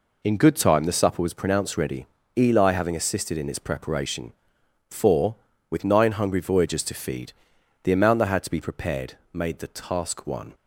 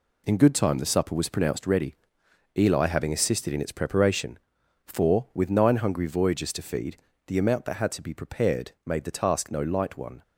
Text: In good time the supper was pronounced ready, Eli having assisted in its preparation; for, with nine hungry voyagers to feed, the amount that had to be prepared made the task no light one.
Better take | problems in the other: second | pauses between "prepared" and "made"; slight; at 9.1 s; 0.18 s long // skips "no light"; at 10.2 s

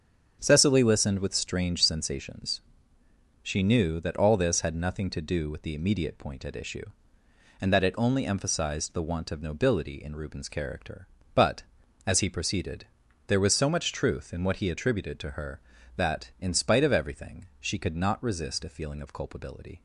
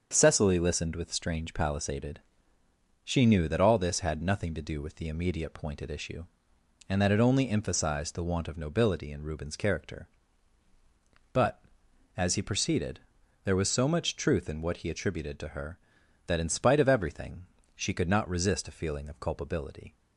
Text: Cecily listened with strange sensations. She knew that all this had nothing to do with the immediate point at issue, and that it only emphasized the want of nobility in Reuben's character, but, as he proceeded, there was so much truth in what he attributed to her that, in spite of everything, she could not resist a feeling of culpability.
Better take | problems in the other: first | starts louder than the rest; strong; until 1.1 s; 7 dB; also in the first // says "palisaded" for "sensations"; at 1.5 s

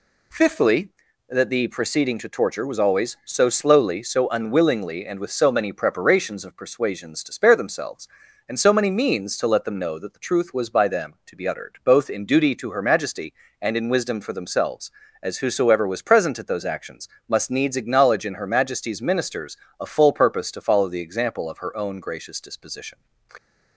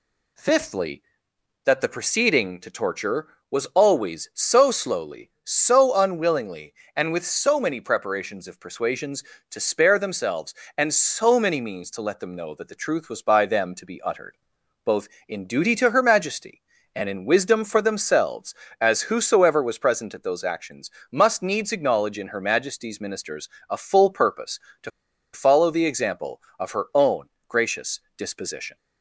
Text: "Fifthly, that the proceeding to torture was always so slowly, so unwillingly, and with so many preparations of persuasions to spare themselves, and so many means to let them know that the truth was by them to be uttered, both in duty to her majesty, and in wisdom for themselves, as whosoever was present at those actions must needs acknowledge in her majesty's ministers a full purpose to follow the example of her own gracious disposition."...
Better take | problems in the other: first | pauses between "actions" and "must"; slight; at 20.8 s; 0.20 s long; slight in the first // pauses between "ministers" and "a"; slight; at 23.4 s; 0.18 s long; slight in the first // pauses between "to" and "follow"; at 24.8 s; 0.43 s long // pauses between "own" and "gracious"; slight; at 27.2 s; 0.18 s long // pauses between "gracious" and "disposition"; slight; at 28.0 s; 0.16 s long

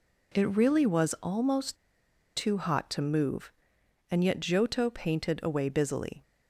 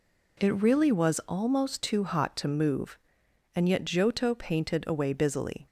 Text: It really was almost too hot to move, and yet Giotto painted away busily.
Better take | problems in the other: second | pauses between "almost" and "too"; noticeable; at 1.7 s; 0.59 s long

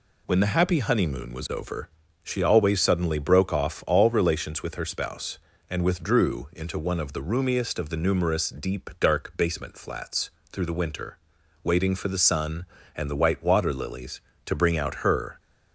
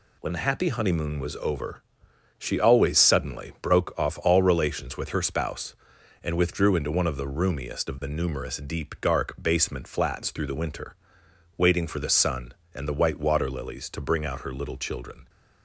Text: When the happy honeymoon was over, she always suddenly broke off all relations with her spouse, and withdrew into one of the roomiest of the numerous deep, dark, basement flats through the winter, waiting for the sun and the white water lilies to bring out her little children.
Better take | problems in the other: second | pauses between "flats" and "through"; slight; at 10.2 s; 0.22 s long // stops before "little children"; at 15.3 s

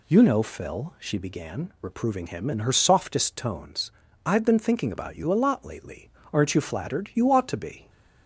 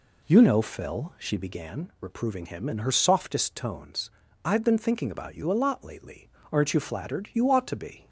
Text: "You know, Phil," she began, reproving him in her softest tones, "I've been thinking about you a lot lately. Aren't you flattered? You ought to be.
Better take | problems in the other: first | starts louder than the rest; slight; until 1.8 s; 3 dB

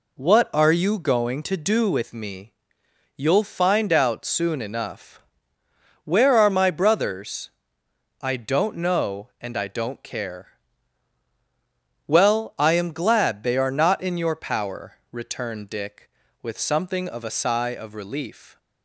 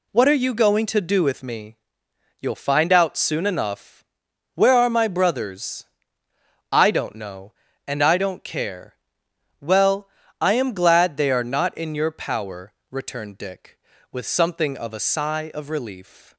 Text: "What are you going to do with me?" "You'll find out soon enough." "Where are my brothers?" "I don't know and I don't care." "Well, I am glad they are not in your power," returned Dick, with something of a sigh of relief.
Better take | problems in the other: neither | none

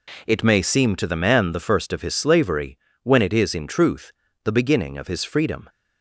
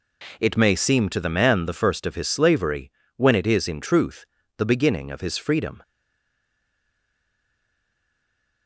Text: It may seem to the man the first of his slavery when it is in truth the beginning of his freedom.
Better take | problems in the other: first | pauses between "slavery" and "when"; slight; at 2.9 s; 0.26 s long; slight in the first // pauses between "truth" and "the"; slight; at 4.2 s; 0.32 s long; slight in the first // stays silent after the last word; strong; from 5.8 s on; 2.8 s long

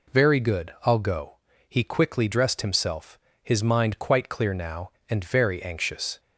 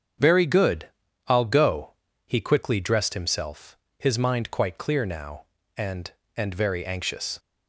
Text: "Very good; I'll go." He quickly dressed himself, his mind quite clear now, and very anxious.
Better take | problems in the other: first | starts louder than the rest; strong; until 1.5 s; 7.5 dB // says "and" twice; at 6.3 s

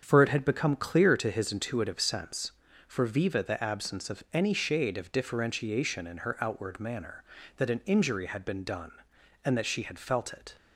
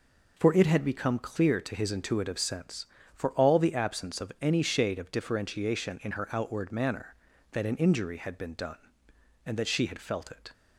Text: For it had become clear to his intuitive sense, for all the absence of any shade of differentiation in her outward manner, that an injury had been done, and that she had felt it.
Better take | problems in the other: second | starts louder than the rest; until 1.0 s; 7 dB // says "viva" for "all"; at 3.0 s

